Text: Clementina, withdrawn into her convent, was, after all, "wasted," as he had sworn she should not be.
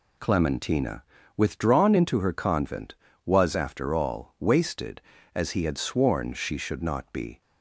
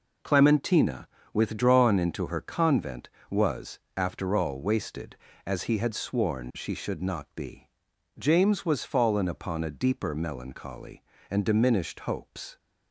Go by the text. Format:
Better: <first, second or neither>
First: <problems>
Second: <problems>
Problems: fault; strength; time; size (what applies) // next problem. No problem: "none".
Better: first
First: none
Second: goes on to say "James was fallen upon a deeper melancholy and diminished hopes"; strong; from 8.1 s on; 4.4 s long